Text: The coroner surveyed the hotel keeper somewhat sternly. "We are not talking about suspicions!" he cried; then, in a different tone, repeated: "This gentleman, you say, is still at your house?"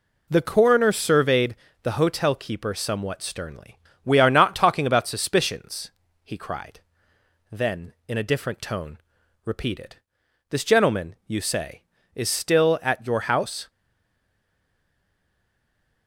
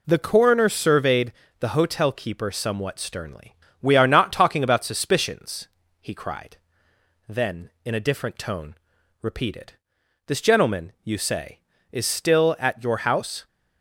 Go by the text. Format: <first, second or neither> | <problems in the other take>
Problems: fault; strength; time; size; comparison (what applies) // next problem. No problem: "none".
second | pauses between "surveyed" and "the"; slight; at 1.5 s; 0.28 s long; slight in the second // stays silent after the last word; from 13.6 s on; 2.4 s long